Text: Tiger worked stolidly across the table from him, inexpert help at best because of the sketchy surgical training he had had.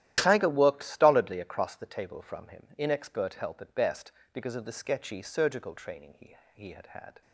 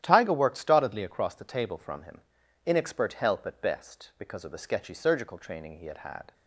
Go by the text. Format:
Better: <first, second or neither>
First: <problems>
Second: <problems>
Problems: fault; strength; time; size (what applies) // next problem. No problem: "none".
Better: second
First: starts louder than the rest; strong; until 1.1 s; 12.5 dB // says "he" twice; at 6.5 s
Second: starts louder than the rest; strong; until 1.0 s; 11.5 dB